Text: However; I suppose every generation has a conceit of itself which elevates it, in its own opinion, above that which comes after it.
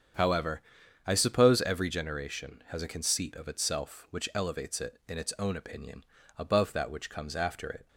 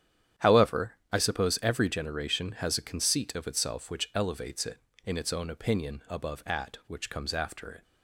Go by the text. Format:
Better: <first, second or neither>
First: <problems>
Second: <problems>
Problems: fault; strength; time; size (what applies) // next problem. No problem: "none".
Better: first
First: starts louder than the rest; strong; until 1.6 s; 8 dB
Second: starts louder than the rest; strong; until 1.5 s; 10 dB // says "at" for "that"; at 6.4 s